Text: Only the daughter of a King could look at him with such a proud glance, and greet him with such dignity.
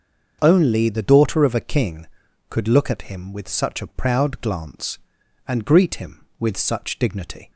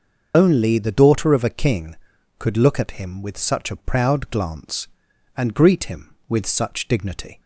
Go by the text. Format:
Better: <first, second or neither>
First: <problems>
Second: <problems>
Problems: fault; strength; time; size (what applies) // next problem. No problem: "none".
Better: first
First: starts louder than the rest; until 1.4 s; 6.5 dB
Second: loses the start of "Only"; at 0.3 s; 50 ms // starts louder than the rest; until 1.3 s; 6.5 dB